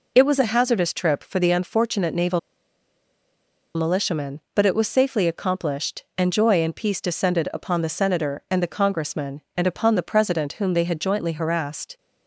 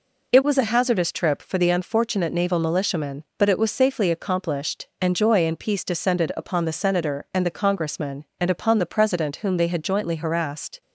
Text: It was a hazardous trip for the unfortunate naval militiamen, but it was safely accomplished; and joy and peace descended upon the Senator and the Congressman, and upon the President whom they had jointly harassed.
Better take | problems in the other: second | pauses between "naval" and "militiamen"; strong; at 2.3 s; 1.3 s long

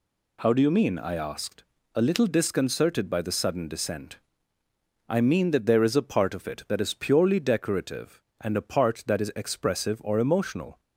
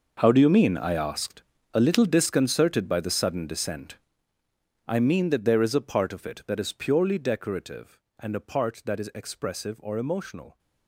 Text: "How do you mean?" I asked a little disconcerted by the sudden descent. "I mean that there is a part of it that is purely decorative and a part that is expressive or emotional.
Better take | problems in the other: first | gets quieter; strong; throughout; 16 dB // pauses between "asked" and "a"; slight; at 1.4 s; 0.30 s long; slight in the first

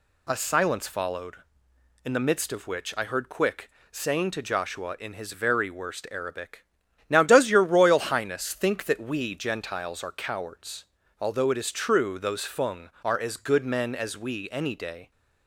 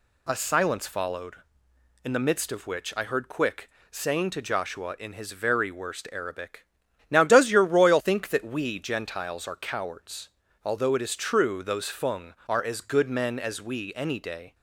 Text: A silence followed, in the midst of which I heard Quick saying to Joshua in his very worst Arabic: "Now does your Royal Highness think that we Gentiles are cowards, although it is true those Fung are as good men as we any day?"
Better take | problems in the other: first | pauses between "Quick" and "saying"; slight; at 3.6 s; 0.20 s long; slight in the first // skips "Highness"; at 8.0 s

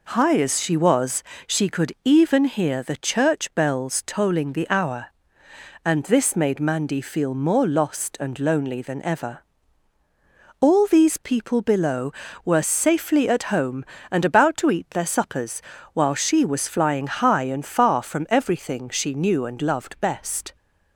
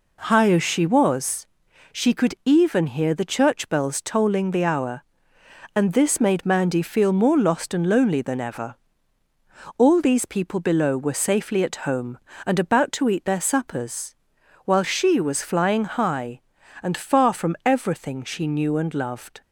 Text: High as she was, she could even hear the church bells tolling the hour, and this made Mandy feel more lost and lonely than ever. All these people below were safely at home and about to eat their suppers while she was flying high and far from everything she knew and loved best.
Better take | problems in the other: first | pauses between "suppers" and "while"; noticeable; at 14.1 s; 0.50 s long; slight in the first // stops before "best"; at 19.4 s

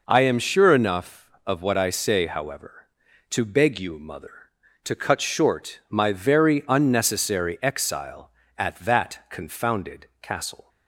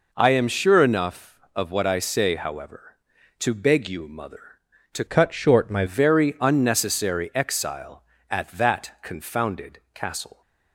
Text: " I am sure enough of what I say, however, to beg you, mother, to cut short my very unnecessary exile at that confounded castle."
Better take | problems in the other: first | changes voice from "cut" to "my"; from 5.0 to 5.8 s; 0.8 s long

